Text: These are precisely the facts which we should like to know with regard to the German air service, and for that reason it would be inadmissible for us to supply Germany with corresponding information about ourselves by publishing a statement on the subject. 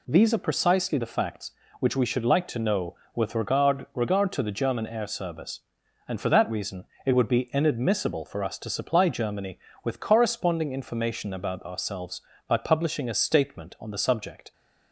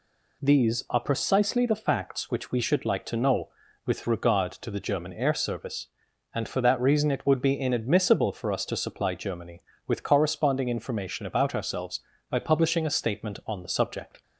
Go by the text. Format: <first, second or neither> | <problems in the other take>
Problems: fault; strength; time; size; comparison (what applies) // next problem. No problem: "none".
second | says "regard" twice; at 3.9 s // pauses between "reason" and "it"; slight; at 6.8 s; 0.20 s long